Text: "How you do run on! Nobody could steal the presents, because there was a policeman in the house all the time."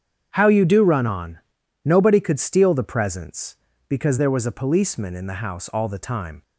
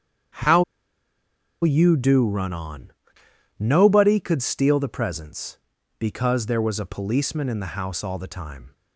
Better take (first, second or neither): first